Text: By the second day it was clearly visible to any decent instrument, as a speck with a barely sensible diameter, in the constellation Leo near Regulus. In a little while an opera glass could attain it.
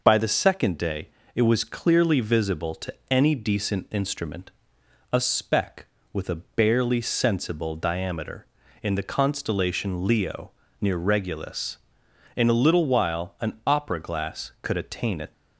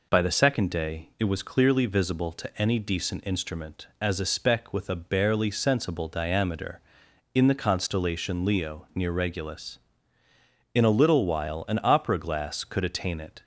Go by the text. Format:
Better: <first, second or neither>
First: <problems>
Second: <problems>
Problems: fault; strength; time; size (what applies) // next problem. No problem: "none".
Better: second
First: pauses between "day" and "it"; slight; at 1.0 s; 0.26 s long // pauses between "to" and "any"; slight; at 2.9 s; 0.16 s long // skips "as"; at 4.8 s // pauses between "Leo" and "near"; slight; at 10.5 s; 0.30 s long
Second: none